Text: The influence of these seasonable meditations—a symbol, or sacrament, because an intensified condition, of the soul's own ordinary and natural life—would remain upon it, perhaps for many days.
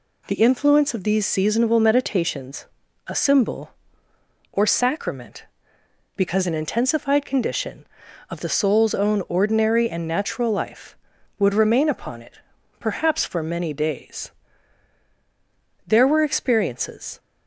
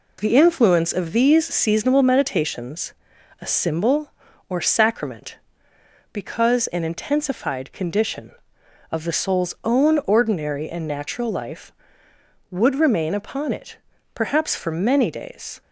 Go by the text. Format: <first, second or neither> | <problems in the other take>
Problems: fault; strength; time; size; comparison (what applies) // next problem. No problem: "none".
second | goes on to say "There were experiences"; from 15.8 s on; 1.3 s long